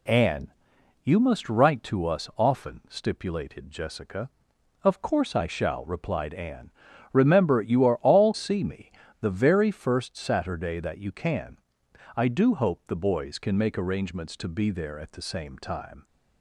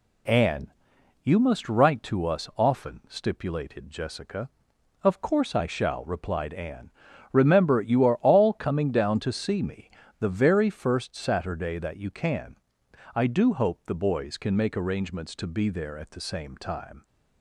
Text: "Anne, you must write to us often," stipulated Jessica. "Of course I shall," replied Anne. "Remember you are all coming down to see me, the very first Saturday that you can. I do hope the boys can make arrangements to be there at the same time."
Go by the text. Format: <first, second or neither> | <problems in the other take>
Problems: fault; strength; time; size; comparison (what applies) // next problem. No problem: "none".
second | skips "coming down to"; at 8.3 s